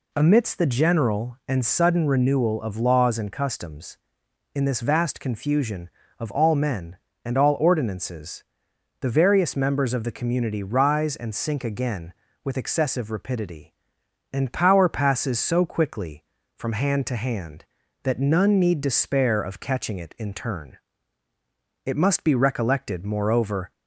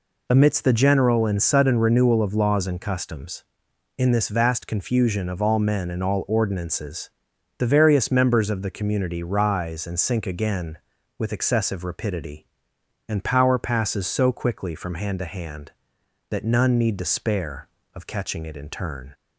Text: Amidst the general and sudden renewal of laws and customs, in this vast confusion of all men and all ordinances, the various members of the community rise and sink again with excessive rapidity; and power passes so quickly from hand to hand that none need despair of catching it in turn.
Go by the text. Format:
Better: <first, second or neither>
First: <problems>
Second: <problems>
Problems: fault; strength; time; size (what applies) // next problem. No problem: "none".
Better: second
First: goes on to say "It must be recollected moreover"; strong; from 21.8 s on; 1.8 s long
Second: none